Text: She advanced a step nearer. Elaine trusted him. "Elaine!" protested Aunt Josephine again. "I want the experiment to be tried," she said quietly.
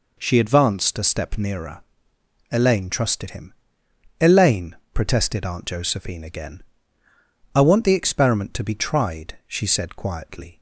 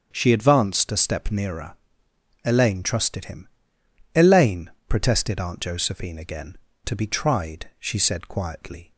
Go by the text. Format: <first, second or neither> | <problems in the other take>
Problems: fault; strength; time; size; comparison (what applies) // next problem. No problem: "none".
first | starts louder than the rest; strong; until 1.1 s; 7.5 dB // skips "I want the experiment"; at 6.7 s